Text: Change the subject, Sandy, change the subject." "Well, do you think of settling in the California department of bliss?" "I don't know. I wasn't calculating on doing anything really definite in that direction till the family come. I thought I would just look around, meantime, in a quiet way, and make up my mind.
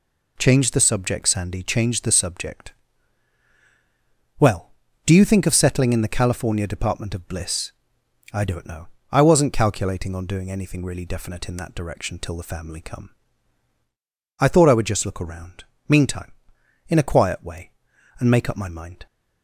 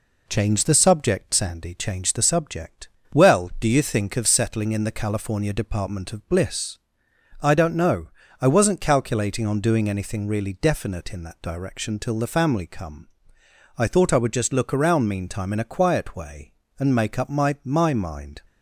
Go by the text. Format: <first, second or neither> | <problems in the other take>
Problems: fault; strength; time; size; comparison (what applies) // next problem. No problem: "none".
first | says "my" twice; at 17.6 s